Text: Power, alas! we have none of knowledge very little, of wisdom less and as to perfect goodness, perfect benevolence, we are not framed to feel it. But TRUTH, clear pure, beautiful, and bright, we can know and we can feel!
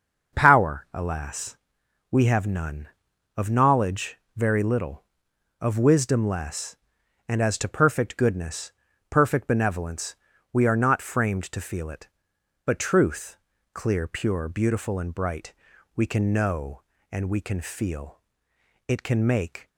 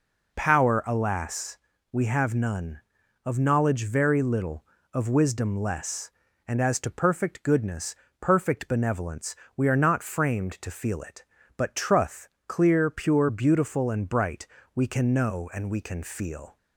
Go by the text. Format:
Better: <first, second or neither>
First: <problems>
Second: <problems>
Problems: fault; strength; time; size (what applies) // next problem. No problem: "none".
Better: second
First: starts louder than the rest; until 1.4 s; 6.5 dB // pauses between "knowledge" and "very"; slight; at 4.1 s; 0.18 s long // goes on to say "It can make"; noticeable; from 18.8 s on; 0.80 s long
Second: none